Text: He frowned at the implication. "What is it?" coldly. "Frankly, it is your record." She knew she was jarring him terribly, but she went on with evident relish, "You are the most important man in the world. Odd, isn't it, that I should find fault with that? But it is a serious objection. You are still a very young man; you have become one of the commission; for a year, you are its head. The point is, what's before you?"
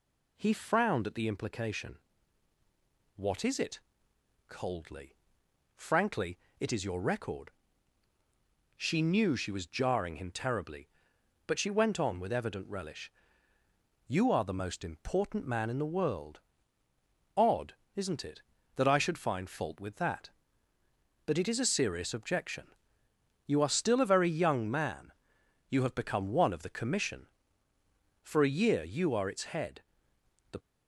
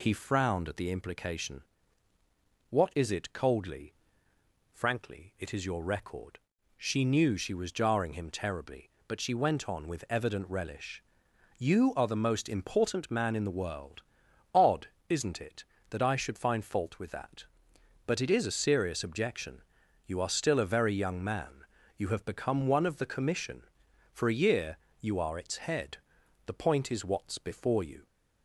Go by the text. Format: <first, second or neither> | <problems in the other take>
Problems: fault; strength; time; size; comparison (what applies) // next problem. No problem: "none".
second | stops before "point is what's before you"; at 30.5 s